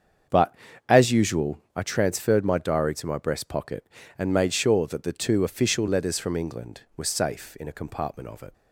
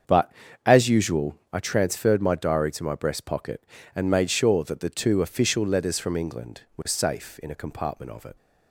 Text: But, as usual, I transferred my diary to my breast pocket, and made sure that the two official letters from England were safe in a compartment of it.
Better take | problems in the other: neither | starts louder than the rest; strong; the same in both

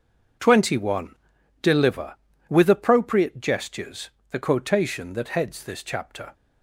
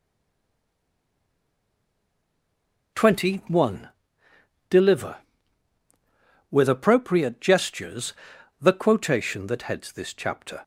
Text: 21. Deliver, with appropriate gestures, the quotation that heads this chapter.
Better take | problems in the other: first | stays silent before the first word; strong; until 2.9 s; 2.9 s long

